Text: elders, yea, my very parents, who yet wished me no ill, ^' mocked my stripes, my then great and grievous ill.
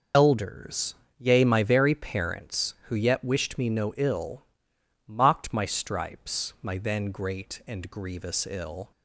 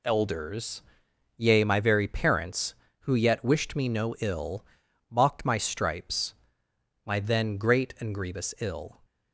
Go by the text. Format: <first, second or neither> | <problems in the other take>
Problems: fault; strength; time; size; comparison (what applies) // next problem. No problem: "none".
second | loses the start of "elders"; at 0.1 s; 60 ms